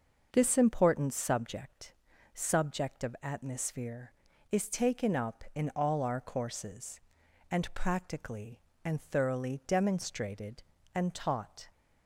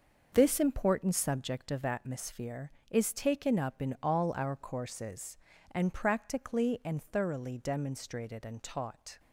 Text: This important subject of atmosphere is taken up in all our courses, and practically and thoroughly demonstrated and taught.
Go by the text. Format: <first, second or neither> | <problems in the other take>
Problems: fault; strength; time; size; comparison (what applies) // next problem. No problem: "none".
second | starts louder than the rest; noticeable; until 1.3 s; 6 dB; also in the second // says "subject" twice; at 2.3 s